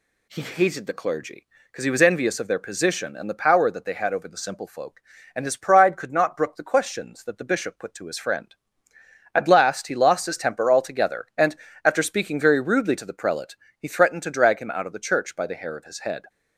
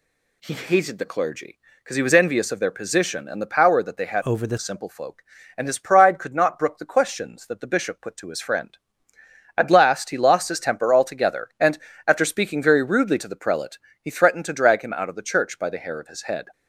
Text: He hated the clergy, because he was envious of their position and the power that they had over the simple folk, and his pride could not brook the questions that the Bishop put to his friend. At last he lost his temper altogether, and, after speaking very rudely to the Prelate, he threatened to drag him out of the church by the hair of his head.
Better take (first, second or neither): first